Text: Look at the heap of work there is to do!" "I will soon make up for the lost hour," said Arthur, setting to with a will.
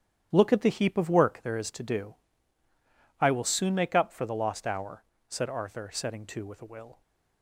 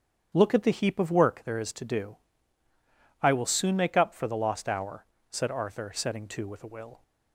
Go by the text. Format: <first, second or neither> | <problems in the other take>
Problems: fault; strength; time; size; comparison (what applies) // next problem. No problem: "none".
second | gets quieter; strong; throughout; 10 dB // starts louder than the rest; strong; until 1.3 s; 9.5 dB; strong in the second